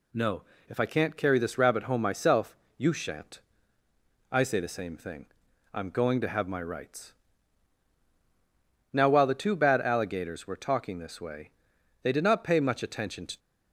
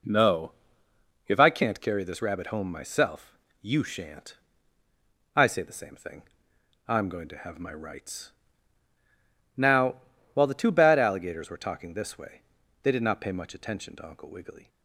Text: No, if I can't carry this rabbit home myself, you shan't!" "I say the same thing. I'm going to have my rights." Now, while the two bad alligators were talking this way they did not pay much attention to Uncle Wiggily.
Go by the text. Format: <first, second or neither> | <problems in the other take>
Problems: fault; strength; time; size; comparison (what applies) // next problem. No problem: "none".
second | pauses between "way" and "they"; noticeable; at 11.5 s; 0.52 s long; also in the second // stops before "Uncle Wiggily"; at 13.3 s